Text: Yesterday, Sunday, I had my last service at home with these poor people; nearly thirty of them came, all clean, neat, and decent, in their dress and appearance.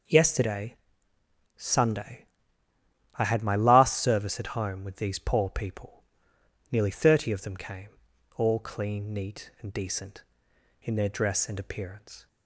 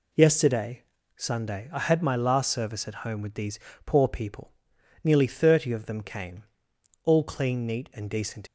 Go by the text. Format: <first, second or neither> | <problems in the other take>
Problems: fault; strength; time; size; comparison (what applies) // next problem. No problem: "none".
first | pauses between "these" and "poor"; slight; at 3.5 s; 0.28 s long // stops before "in their dress and appearance"; at 8.4 s